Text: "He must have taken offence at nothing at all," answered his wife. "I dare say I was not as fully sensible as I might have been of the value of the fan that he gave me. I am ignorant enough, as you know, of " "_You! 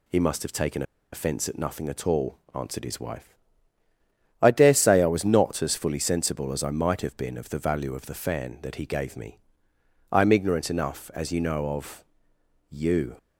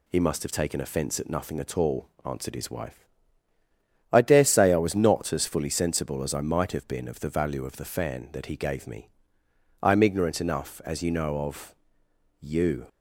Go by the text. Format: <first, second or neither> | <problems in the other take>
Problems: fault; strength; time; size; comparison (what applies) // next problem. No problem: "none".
second | pauses between "taken" and "offence"; slight; at 0.8 s; 0.30 s long